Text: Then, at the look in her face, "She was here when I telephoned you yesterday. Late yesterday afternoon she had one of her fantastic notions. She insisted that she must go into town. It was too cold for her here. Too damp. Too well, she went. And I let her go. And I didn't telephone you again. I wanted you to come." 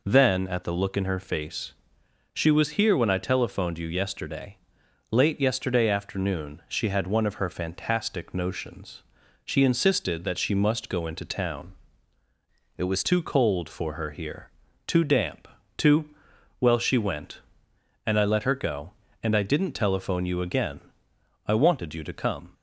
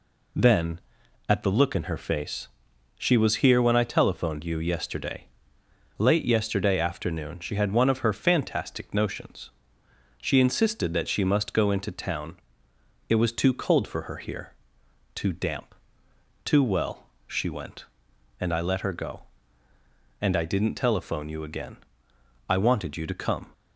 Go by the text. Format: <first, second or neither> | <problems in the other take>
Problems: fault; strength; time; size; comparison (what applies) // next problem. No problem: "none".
second | changes voice from "It" to "was"; from 12.7 to 13.0 s; 0.3 s long // pauses between "Too" and "well"; noticeable; at 16.0 s; 0.52 s long